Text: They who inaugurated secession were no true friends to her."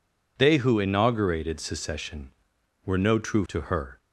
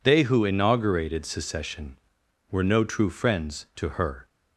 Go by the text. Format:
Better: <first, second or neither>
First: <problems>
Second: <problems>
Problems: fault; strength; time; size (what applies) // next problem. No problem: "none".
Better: second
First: skips "friends"; at 3.4 s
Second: none